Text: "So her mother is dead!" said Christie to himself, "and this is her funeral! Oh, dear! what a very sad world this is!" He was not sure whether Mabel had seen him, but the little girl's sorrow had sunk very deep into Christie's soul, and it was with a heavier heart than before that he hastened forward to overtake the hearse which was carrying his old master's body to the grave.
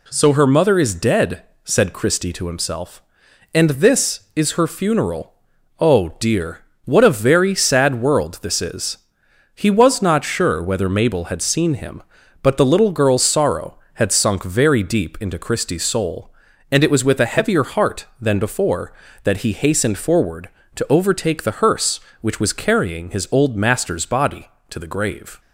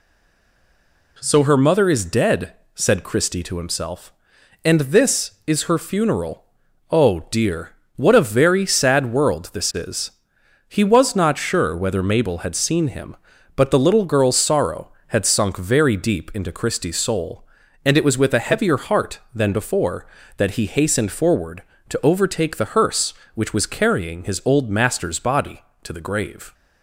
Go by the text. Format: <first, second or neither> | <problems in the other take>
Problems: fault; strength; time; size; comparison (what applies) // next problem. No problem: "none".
first | stays silent before the first word; until 1.1 s; 1.1 s long